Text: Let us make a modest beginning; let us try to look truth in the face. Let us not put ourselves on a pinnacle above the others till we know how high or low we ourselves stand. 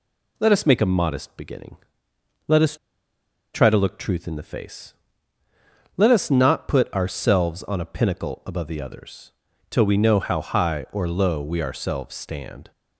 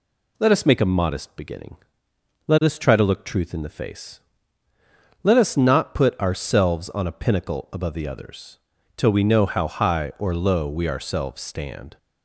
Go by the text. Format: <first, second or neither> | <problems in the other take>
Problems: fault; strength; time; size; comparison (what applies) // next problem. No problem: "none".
second | pauses between "us" and "try"; noticeable; at 2.7 s; 0.78 s long // pauses between "others" and "till"; at 9.3 s; 0.38 s long; also in the second